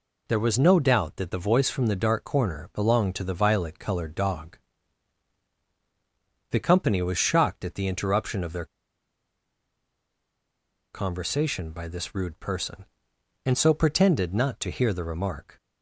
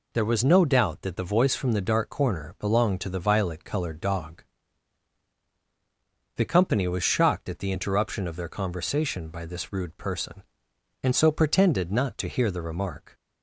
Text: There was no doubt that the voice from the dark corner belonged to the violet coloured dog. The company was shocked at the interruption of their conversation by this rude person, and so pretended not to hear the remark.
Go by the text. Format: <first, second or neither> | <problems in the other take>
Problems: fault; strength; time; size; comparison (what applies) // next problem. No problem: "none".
second | pauses between "their" and "conversation"; strong; at 8.6 s; 2.2 s long